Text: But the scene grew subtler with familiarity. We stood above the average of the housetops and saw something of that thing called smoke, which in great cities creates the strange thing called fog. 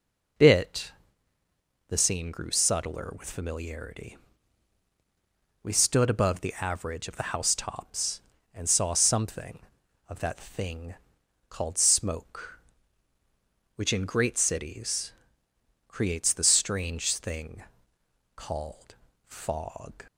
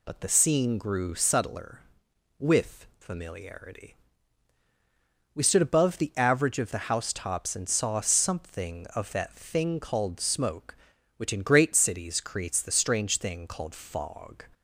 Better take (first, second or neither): second